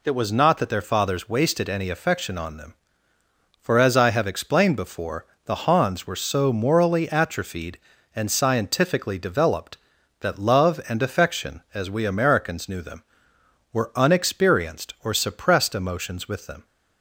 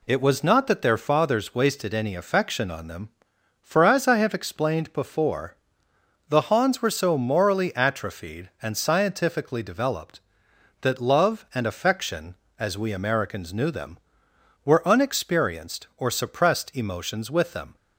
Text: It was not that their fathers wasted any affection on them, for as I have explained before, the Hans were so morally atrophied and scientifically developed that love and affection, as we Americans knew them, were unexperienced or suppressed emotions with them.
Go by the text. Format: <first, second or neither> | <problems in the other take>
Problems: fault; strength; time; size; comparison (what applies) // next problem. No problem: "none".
neither | none